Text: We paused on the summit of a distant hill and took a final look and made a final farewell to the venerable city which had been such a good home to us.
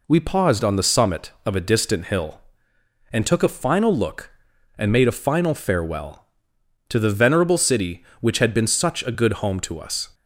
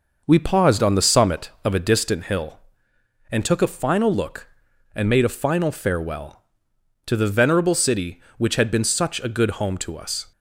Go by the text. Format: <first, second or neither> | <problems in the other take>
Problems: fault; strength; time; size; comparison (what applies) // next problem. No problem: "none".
first | starts louder than the rest; noticeable; until 2.1 s; 6 dB